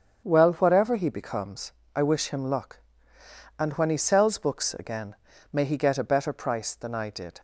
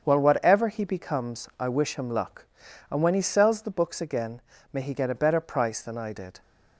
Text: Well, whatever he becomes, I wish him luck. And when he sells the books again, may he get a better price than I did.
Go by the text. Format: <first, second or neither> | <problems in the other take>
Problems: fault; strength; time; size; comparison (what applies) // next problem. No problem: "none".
second | starts louder than the rest; strong; until 1.2 s; 7.5 dB; also in the second // skips "the"; at 4.3 s